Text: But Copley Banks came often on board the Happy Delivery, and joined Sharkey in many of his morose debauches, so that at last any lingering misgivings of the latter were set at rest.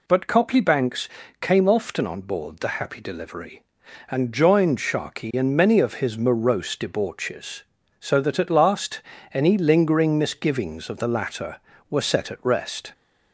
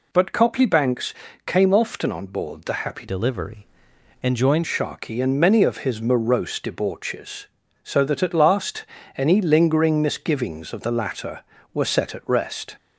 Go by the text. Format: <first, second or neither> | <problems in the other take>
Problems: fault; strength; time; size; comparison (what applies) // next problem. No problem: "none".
first | pauses between "Banks" and "came"; slight; at 1.1 s; 0.32 s long; slight in the first // changes voice from "Delivery" to "joined"; from 3.0 to 4.6 s; 1.6 s long // pauses between "last" and "any"; slight; at 8.8 s; 0.32 s long; slight in the first